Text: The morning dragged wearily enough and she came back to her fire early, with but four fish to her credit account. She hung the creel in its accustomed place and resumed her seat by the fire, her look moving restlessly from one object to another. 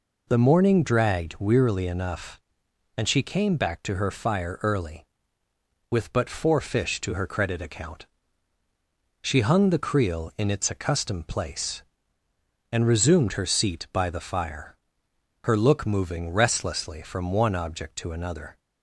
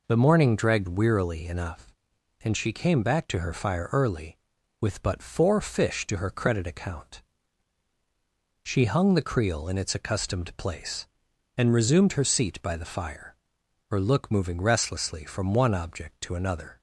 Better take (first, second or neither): neither